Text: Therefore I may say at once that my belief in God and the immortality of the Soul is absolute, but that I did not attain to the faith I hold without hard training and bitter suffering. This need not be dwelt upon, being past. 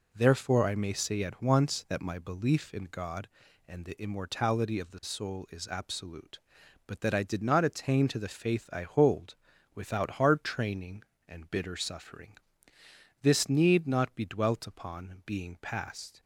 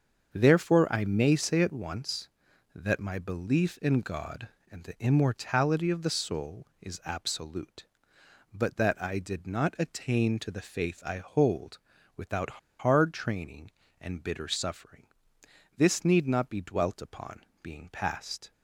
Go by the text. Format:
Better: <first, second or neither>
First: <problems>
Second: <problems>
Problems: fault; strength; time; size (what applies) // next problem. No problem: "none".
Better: first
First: pauses between "hold" and "without"; at 9.3 s; 0.38 s long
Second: starts louder than the rest; until 1.3 s; 7 dB // pauses between "hold" and "without"; at 11.7 s; 0.38 s long // pauses between "without" and "hard"; slight; at 12.5 s; 0.22 s long